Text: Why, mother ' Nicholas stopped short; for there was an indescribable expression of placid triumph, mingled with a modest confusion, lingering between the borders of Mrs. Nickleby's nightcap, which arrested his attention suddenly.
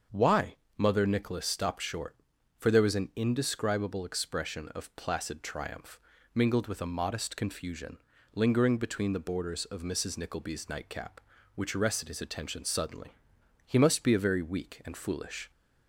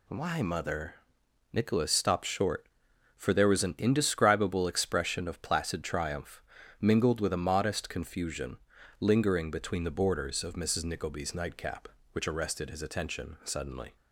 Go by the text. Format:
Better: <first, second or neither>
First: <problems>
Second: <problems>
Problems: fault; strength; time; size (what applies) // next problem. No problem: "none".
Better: second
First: starts louder than the rest; until 1.3 s; 7 dB // goes on to say "He must be a very weak and foolish"; strong; from 13.6 s on; 1.8 s long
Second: none